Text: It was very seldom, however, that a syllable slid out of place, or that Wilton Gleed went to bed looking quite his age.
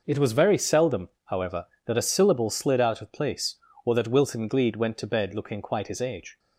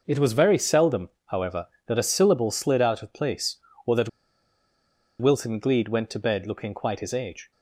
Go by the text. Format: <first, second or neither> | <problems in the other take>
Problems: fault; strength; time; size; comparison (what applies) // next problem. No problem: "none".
first | pauses between "that" and "Wilton"; at 4.0 s; 1.1 s long